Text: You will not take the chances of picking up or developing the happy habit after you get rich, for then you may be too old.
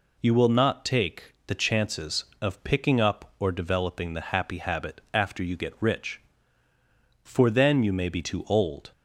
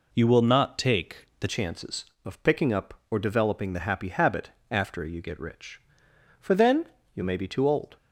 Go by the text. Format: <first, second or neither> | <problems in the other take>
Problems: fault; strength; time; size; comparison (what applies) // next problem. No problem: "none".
first | changes voice at "chances"; from 1.4 s on; 6.5 s long // pauses between "habit" and "after"; slight; at 4.5 s; 0.20 s long // pauses between "then" and "you"; slight; at 6.8 s; 0.30 s long